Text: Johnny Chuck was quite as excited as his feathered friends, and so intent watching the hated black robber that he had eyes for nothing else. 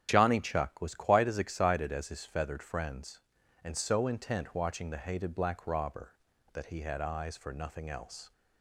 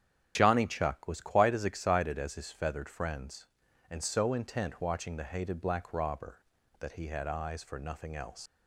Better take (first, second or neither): first